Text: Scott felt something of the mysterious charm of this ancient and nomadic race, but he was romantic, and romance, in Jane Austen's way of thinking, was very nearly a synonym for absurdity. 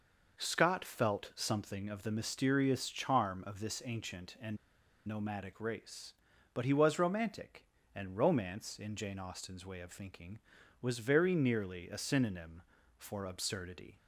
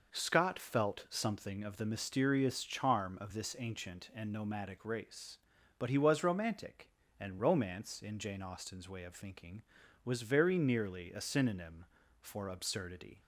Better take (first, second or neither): second